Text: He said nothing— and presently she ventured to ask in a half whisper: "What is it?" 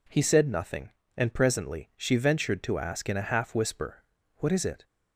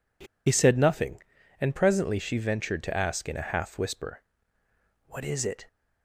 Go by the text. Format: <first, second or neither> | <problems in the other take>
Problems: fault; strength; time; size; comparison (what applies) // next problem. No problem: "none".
first | pauses between "He" and "said"; slight; at 0.2 s; 0.22 s long